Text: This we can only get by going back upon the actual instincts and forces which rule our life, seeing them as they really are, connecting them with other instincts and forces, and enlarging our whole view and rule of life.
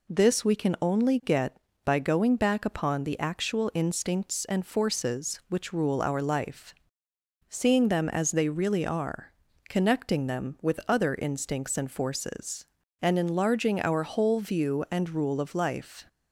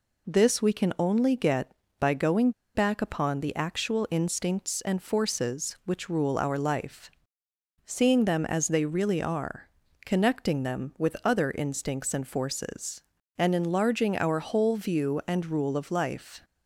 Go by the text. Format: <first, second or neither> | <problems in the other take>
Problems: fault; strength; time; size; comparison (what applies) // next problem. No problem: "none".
first | pauses between "going" and "back"; slight; at 2.5 s; 0.24 s long